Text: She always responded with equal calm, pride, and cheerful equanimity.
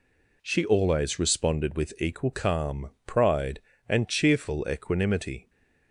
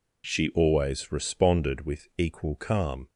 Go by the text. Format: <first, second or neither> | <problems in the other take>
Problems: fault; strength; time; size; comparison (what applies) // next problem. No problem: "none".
first | stops before "pride and cheerful equanimity"; at 3.0 s